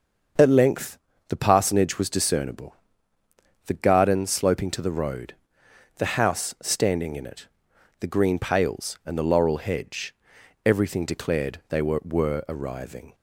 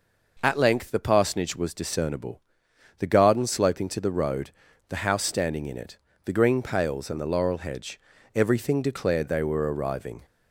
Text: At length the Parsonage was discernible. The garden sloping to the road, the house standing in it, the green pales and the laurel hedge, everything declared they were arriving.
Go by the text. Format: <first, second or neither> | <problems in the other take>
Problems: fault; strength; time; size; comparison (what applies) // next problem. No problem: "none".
second | starts louder than the rest; until 1.6 s; 6.5 dB // pauses between "length" and "the"; slight; at 0.9 s; 0.30 s long // says "were" twice; at 12.0 s